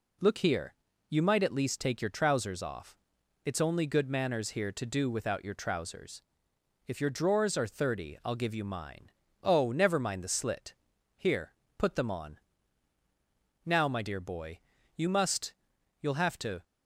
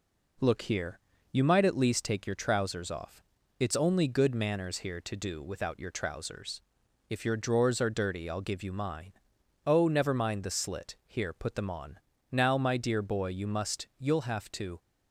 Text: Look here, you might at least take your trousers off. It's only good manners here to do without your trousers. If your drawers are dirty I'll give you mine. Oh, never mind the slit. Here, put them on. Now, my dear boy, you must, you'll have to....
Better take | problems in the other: second | says "thirty" for "dirty"; at 7.6 s

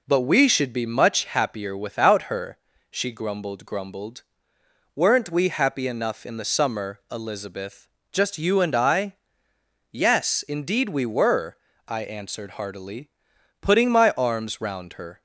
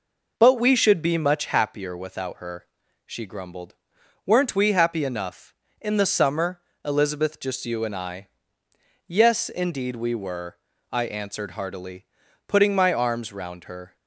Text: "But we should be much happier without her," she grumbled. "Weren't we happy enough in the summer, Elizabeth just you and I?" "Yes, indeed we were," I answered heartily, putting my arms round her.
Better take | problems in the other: second | says "grumbled" twice; at 3.6 s // pauses between "Elizabeth" and "just"; slight; at 7.8 s; 0.24 s long

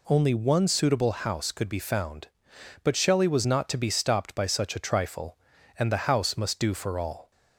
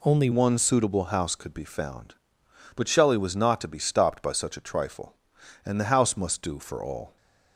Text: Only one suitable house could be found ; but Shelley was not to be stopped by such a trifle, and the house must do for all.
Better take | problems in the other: first | changes voice at "one"; from 0.3 s on; 6.8 s long

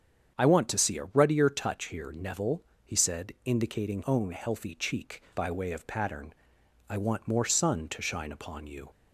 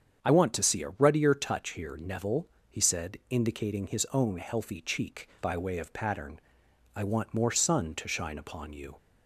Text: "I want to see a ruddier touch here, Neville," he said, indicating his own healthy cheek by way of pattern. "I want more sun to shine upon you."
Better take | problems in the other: second | starts louder than the rest; strong; until 1.4 s; 8 dB; strong in the second // skips "his"; at 4.0 s

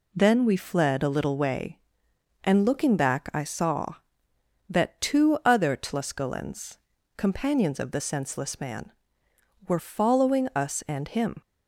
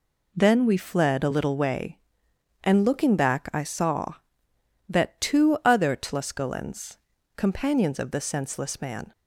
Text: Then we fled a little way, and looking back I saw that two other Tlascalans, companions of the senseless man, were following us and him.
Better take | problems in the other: first | stops before "were following us and him"; at 9.1 s

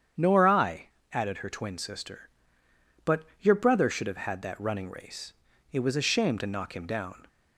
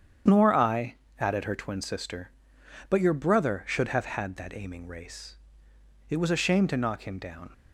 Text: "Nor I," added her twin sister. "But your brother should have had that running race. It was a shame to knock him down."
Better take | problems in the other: first | starts louder than the rest; strong; until 1.5 s; 8.5 dB; strong in the first // says "aiming" for "running"; at 4.5 s

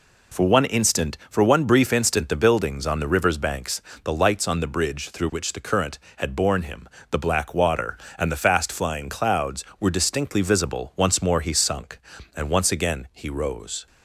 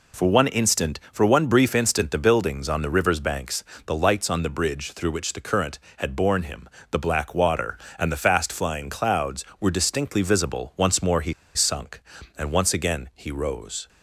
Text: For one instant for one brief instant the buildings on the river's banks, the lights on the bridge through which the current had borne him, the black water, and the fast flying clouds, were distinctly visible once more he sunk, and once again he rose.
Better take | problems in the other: first | pauses between "he" and "sunk"; slight; at 11.3 s; 0.22 s long

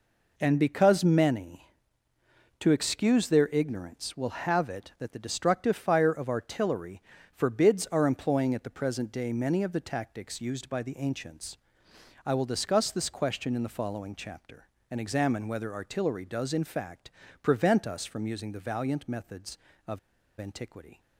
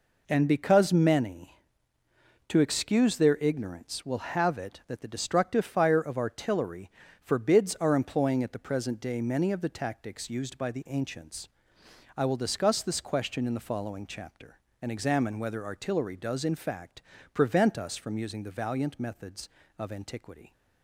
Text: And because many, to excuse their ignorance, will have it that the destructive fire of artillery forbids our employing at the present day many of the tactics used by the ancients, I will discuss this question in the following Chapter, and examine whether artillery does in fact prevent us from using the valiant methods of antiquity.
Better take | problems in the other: second | pauses between "artillery" and "forbids"; slight; at 7.0 s; 0.34 s long; slight in the second // pauses between "fact" and "prevent"; slight; at 17.1 s; 0.30 s long; slight in the second // pauses between "of" and "antiquity"; at 19.9 s; 0.41 s long

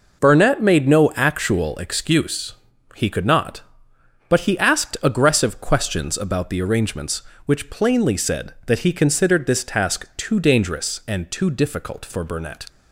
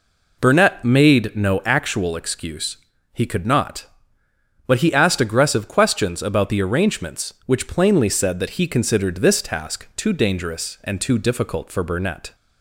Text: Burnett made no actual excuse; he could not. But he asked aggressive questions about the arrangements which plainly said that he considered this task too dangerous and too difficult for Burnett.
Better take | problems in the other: neither | none

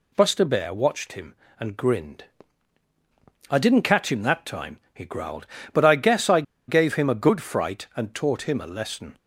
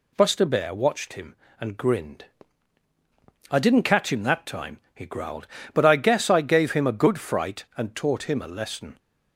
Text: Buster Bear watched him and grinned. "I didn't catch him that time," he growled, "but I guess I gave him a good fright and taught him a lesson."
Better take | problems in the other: second | pauses between "I" and "gave"; slight; at 6.4 s; 0.25 s long

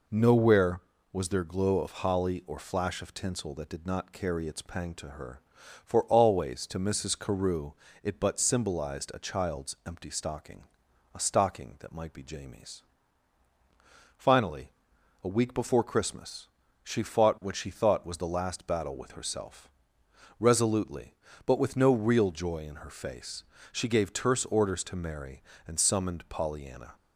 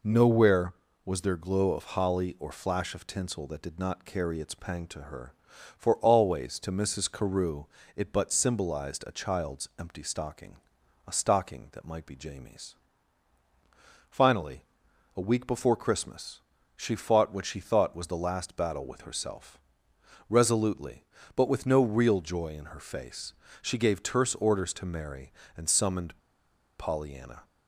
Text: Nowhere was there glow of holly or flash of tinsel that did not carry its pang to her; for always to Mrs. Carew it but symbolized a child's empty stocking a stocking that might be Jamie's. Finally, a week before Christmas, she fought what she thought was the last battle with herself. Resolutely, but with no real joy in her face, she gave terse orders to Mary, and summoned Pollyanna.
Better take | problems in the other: first | pauses between "Carew" and "it"; slight; at 7.6 s; 0.30 s long; slight in the first // pauses between "stocking" and "a"; noticeable; at 10.5 s; 0.50 s long; noticeable in the first // pauses between "summoned" and "Pollyanna"; noticeable; at 26.1 s; 0.61 s long

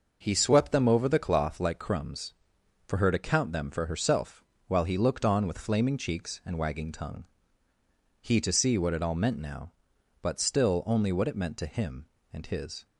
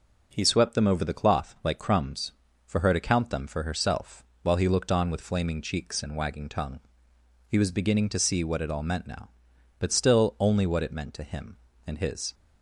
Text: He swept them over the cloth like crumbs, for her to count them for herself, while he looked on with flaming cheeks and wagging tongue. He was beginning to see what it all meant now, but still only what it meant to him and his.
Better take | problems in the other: second | skips "was beginning"; at 8.4 s

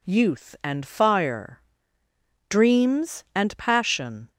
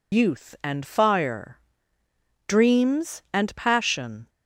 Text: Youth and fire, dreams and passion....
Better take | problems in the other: first | loses the start of "Youth"; at 0.1 s; 80 ms

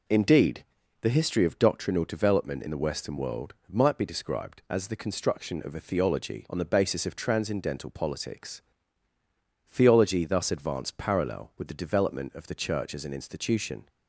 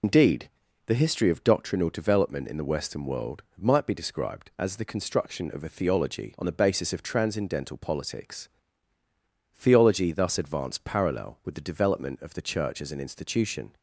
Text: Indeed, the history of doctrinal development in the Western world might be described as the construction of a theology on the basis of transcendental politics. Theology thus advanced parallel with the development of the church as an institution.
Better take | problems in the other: first | loses the start of "Indeed"; at 0.0 s; 100 ms // pauses between "world" and "might"; slight; at 3.4 s; 0.16 s long; slight in the first

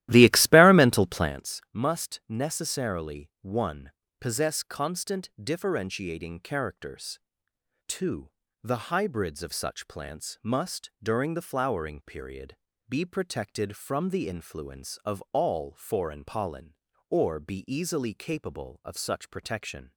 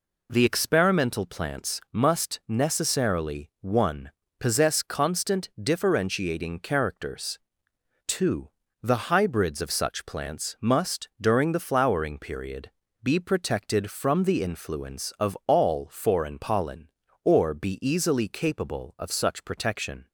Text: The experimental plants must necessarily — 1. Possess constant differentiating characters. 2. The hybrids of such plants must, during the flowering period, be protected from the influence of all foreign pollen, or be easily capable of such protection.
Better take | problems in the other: second | starts louder than the rest; strong; until 1.4 s; 15 dB

